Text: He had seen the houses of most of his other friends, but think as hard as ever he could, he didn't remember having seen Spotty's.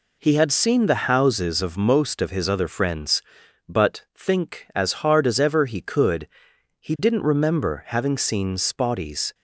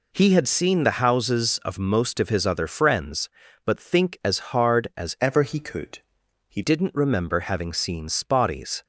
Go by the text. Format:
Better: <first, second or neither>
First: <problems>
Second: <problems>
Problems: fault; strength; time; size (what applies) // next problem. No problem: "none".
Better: first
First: none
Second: changes voice from "ever" to "he"; from 5.2 to 6.6 s; 1.4 s long